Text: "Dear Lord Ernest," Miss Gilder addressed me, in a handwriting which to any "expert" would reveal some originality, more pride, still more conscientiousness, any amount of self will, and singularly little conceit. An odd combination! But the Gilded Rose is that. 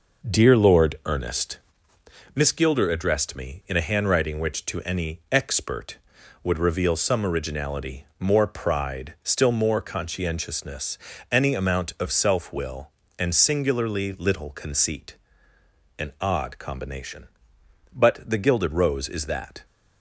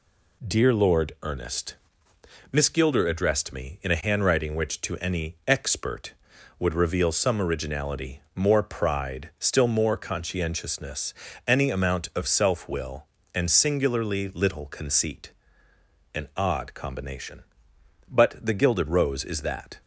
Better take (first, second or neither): second